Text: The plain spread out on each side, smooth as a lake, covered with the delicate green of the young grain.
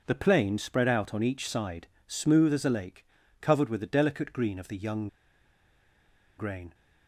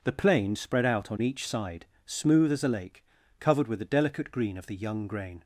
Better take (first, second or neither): second